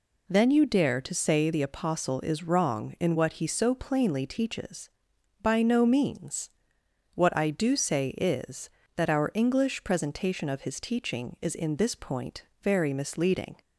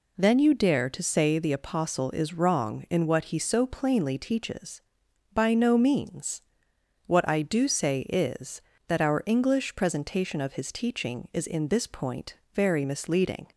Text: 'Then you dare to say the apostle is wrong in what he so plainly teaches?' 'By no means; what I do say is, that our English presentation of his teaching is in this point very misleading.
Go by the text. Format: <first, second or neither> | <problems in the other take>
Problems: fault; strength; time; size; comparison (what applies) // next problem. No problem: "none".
neither | pauses between "point" and "very"; slight; the same in both